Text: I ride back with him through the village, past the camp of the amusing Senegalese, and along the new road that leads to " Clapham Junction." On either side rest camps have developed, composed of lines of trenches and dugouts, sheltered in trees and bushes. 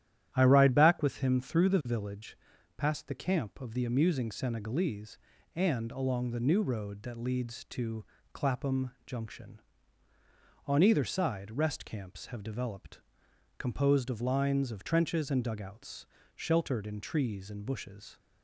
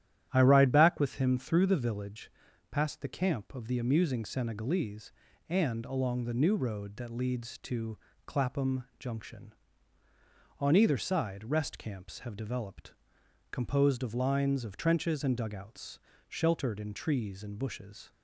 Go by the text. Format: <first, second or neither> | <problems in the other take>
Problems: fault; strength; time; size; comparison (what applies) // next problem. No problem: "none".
neither | starts louder than the rest; strong; the same in both